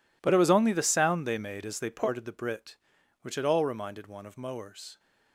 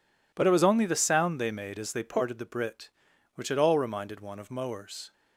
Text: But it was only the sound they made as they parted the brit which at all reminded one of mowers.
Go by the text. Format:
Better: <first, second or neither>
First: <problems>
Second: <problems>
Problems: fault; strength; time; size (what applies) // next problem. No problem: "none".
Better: second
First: gets quieter; strong; throughout; 17.5 dB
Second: none